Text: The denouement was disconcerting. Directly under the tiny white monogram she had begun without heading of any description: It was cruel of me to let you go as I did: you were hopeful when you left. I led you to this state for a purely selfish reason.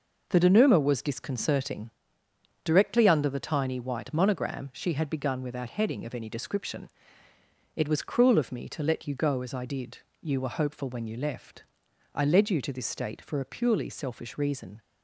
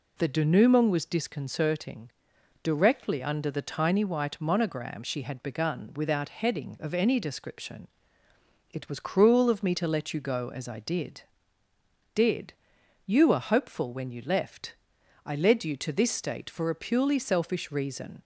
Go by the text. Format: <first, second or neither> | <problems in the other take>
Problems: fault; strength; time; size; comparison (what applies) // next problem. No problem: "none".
first | says "did" twice; at 12.1 s